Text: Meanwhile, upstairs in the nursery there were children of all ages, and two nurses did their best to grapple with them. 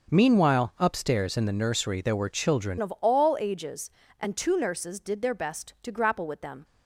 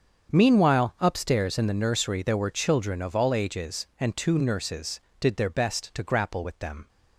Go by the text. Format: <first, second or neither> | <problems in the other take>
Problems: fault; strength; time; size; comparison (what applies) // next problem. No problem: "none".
second | starts louder than the rest; until 1.1 s; 6 dB; strong in the second // changes voice at "of"; from 2.8 s on; 3.8 s long